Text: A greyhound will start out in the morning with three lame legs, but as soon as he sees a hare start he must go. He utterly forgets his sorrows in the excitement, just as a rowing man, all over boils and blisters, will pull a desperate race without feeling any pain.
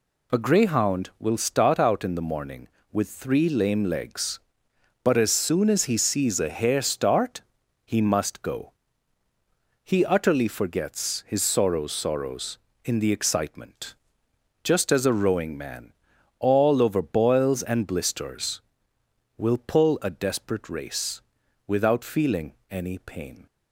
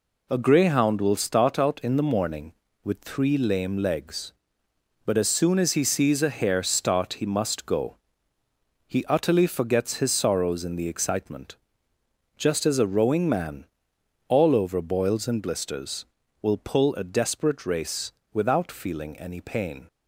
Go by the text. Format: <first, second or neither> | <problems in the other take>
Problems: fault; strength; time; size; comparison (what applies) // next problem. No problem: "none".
second | pauses between "start" and "he"; at 7.4 s; 0.44 s long // says "sorrows" twice; at 11.9 s // pauses between "race" and "without"; noticeable; at 21.2 s; 0.46 s long; slight in the second // pauses between "feeling" and "any"; slight; at 22.5 s; 0.18 s long